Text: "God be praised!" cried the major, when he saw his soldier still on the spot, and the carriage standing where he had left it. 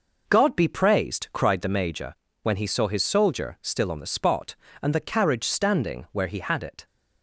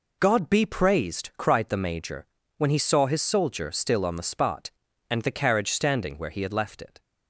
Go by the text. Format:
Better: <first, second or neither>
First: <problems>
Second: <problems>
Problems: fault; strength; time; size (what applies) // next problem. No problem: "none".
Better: second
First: skips "left"; at 6.6 s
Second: none